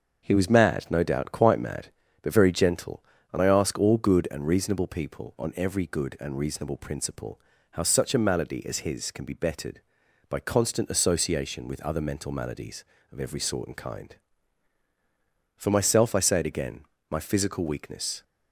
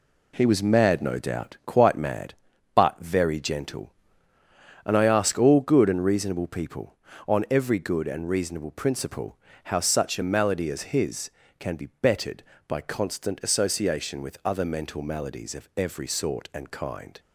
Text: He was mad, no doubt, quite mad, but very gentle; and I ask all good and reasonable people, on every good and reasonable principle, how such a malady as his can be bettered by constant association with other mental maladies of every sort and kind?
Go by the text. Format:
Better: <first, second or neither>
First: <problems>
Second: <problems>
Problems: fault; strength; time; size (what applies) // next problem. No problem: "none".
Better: second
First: starts louder than the rest; until 1.2 s; 7 dB // goes on to say "For myself I say it again my physical weakness"; strong; from 15.5 s on; 2.6 s long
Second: none